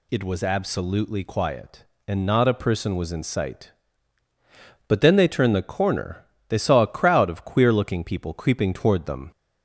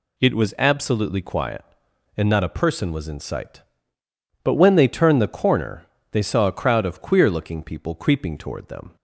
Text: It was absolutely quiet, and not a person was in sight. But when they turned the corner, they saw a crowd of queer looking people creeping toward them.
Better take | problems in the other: second | says "then" for "when"; at 5.0 s

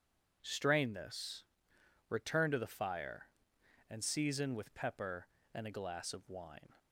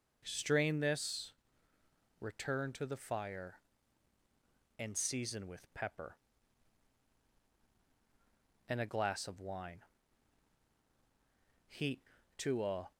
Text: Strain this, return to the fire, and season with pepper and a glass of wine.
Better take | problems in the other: first | goes on to say "Heat to a"; noticeable; from 11.6 s on; 1.2 s long

